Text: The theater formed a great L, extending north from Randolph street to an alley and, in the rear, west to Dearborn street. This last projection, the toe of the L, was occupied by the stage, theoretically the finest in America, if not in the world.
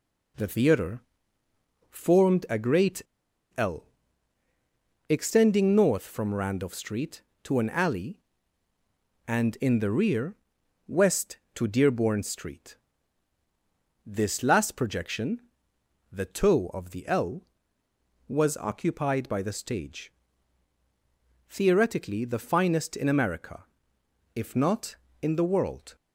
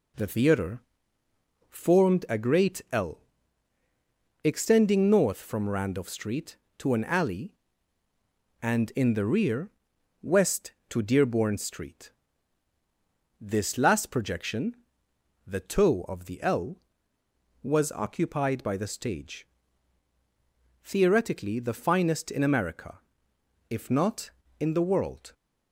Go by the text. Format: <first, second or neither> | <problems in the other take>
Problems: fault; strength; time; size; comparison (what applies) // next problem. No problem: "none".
second | pauses between "theater" and "formed"; noticeable; at 1.0 s; 0.88 s long; noticeable in the second // pauses between "great" and "L"; noticeable; at 3.0 s; 0.54 s long